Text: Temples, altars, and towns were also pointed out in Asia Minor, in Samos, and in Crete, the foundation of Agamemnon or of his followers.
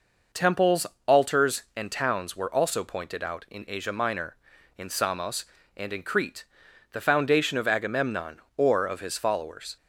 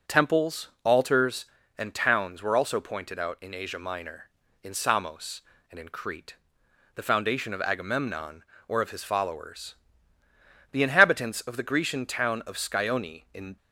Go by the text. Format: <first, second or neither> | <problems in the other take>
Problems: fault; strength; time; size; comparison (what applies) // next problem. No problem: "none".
first | goes on to say "The inhabitants of the Grecian town of Scione in"; strong; from 10.7 s on; 2.8 s long